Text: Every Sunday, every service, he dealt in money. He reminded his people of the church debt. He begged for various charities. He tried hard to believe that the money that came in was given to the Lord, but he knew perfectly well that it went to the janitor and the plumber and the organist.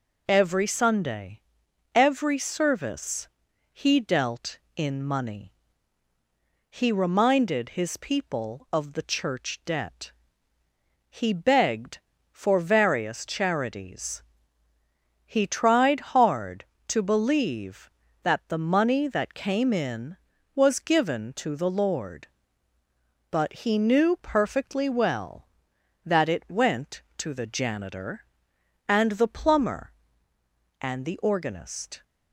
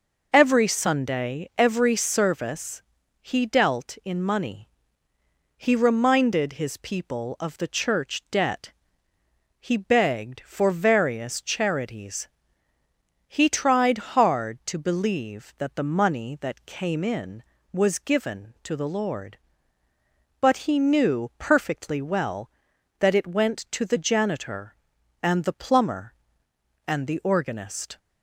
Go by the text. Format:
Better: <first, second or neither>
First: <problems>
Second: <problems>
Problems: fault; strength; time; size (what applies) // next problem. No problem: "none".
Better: neither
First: none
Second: none